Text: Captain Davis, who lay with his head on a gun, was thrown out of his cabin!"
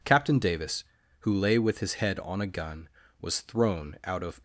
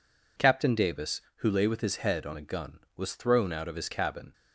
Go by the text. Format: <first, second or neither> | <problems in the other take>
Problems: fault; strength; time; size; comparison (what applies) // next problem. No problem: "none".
second | stops before "his cabin"; at 4.3 s